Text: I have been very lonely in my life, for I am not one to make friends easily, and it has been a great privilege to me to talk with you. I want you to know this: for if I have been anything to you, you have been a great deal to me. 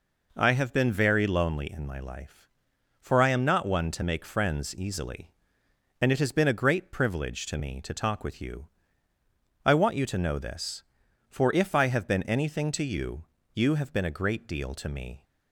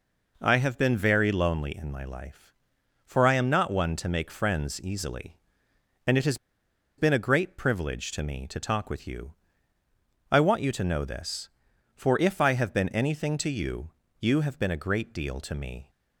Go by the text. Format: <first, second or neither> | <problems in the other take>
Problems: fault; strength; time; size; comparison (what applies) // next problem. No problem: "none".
first | pauses between "has" and "been"; noticeable; at 6.3 s; 0.62 s long